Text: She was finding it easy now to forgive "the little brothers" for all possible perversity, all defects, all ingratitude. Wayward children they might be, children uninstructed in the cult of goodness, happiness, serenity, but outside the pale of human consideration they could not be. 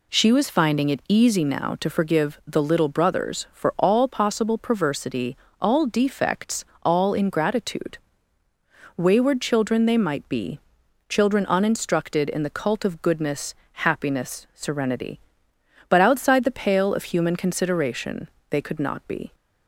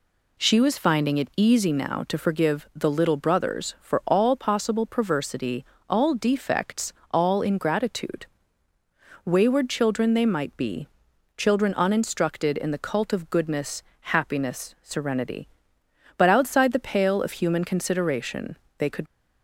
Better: first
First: pauses between "consideration" and "they"; slight; at 18.2 s; 0.22 s long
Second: pauses between "consideration" and "they"; slight; at 18.5 s; 0.22 s long // stops before "not be"; at 19.0 s

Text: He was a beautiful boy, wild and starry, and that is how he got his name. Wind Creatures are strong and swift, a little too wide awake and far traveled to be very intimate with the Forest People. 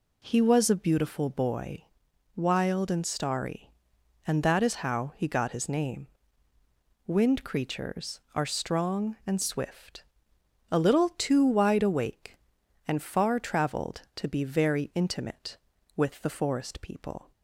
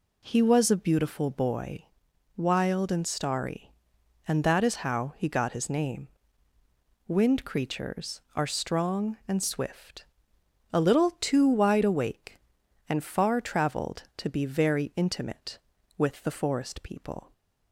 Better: neither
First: none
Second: none

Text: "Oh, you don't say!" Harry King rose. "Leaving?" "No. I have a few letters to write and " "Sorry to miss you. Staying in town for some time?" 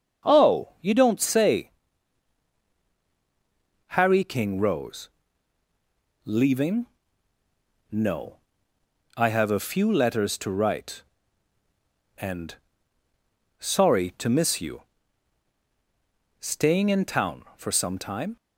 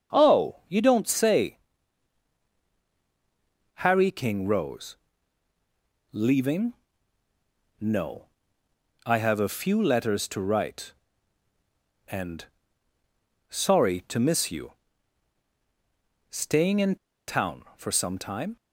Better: first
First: starts louder than the rest; until 1.3 s; 7 dB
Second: starts louder than the rest; until 1.2 s; 7 dB // pauses between "in" and "town"; slight; at 16.9 s; 0.31 s long

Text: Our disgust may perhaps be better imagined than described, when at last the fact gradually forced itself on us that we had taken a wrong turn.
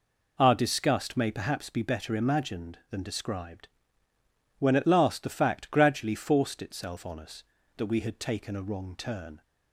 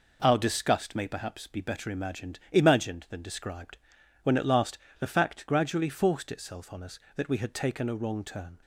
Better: first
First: none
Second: says "imagined" twice; at 2.5 s // pauses between "last" and "the"; slight; at 4.7 s; 0.22 s long

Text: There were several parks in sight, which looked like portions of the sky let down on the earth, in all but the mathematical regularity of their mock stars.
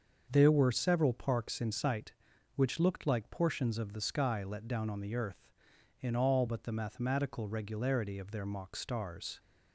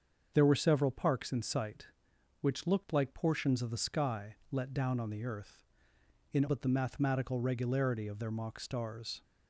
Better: first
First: starts louder than the rest; until 1.3 s; 6.5 dB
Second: starts louder than the rest; until 1.3 s; 7 dB // pauses between "sky" and "let"; slight; at 4.3 s; 0.16 s long // skips "all"; at 6.4 s

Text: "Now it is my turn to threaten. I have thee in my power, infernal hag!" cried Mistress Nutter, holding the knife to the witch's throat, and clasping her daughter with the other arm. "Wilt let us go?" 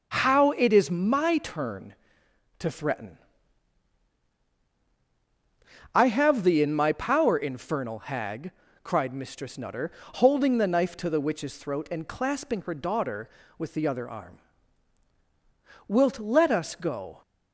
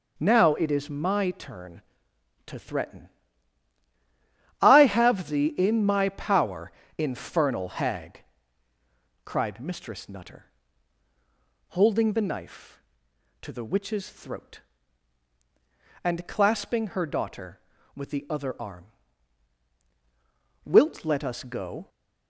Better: second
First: says "How" for "Now"; at 0.0 s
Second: none

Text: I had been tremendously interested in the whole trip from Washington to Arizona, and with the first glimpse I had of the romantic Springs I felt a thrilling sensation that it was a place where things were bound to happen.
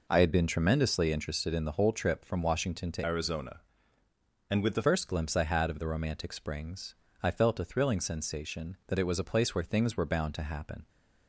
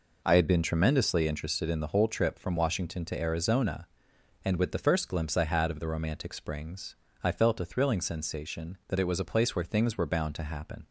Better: second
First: changes voice from "Arizona" to "the"; from 3.0 to 4.8 s; 1.8 s long // pauses between "Springs" and "I"; slight; at 6.9 s; 0.26 s long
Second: pauses between "Springs" and "I"; slight; at 6.9 s; 0.26 s long

